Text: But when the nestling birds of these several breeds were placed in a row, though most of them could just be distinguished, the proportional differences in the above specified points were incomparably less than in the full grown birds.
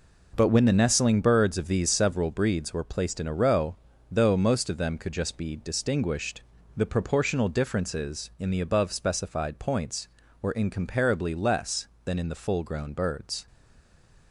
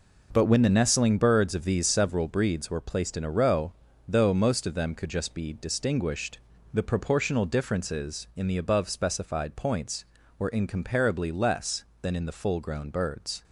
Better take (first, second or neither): second